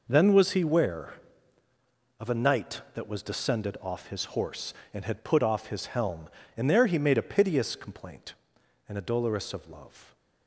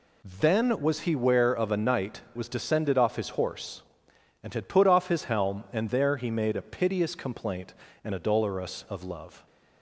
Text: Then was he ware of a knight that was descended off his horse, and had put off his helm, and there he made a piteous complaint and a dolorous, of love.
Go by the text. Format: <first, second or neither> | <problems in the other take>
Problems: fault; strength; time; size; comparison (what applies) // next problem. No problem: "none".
first | skips "that"; at 2.2 s